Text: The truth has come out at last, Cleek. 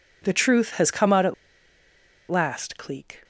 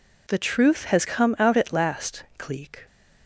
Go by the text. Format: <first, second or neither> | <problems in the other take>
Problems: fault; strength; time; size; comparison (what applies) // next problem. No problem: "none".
second | pauses between "at" and "last"; noticeable; at 1.3 s; 0.95 s long